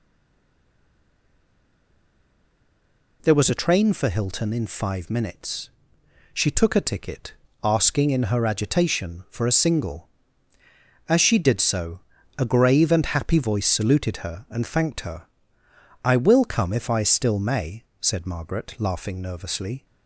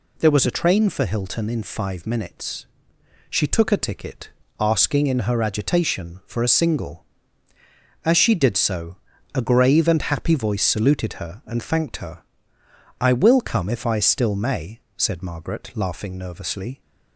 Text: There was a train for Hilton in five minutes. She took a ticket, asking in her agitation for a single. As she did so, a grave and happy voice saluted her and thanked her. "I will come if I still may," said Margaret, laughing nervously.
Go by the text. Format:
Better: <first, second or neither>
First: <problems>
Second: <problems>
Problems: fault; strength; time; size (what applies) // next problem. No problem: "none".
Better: second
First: stays silent before the first word; strong; until 3.1 s; 3.1 s long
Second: none